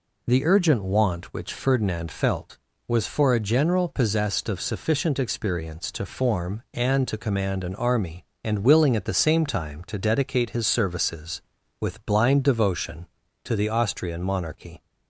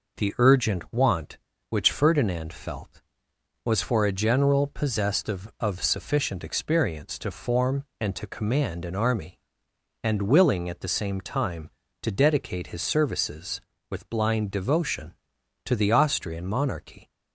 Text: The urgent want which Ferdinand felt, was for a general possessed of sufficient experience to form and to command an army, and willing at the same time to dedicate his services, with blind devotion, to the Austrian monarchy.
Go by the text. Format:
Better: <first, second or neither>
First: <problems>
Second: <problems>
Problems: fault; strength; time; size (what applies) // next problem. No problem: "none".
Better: first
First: none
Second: says "of" twice; at 5.5 s